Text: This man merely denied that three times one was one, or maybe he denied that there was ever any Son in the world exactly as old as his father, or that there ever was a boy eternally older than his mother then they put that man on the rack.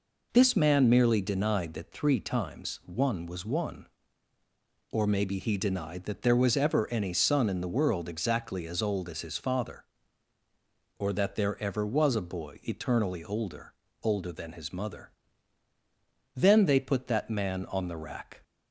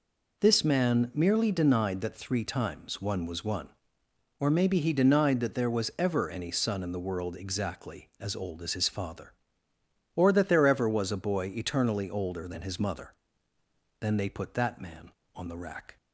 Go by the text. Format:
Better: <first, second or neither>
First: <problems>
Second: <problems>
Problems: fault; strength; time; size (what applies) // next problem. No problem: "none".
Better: second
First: says "older" twice; at 14.0 s // pauses between "mother" and "then"; at 15.1 s; 1.2 s long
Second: pauses between "mother" and "then"; noticeable; at 13.1 s; 0.88 s long